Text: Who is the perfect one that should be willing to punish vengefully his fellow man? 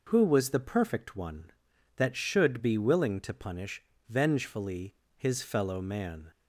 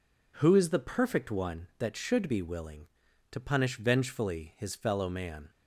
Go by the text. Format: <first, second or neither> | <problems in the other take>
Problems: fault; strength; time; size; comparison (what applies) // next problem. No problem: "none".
second | says "was" for "is"; at 0.2 s // pauses between "punish" and "vengefully"; slight; at 3.8 s; 0.25 s long // pauses between "vengefully" and "his"; slight; at 4.9 s; 0.22 s long